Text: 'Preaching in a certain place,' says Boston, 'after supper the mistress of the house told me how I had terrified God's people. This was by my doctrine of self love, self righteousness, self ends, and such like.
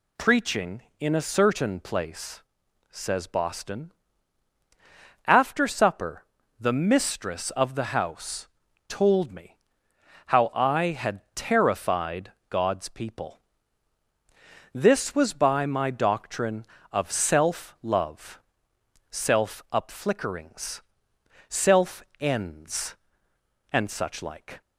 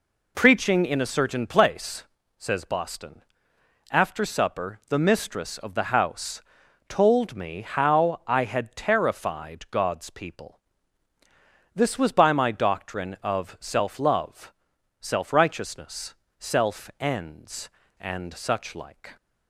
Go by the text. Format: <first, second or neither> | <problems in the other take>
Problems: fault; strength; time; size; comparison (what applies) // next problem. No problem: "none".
second | pauses between "supper" and "the"; slight; at 6.2 s; 0.34 s long // pauses between "house" and "told"; at 8.4 s; 0.42 s long; noticeable in the second // pauses between "me" and "how"; noticeable; at 9.5 s; 0.68 s long // pauses between "terrified" and "God's"; slight; at 12.3 s; 0.16 s long // says "upflickerings" for "righteousness"; at 19.7 s // pauses between "self" and "ends"; slight; at 22.0 s; 0.16 s long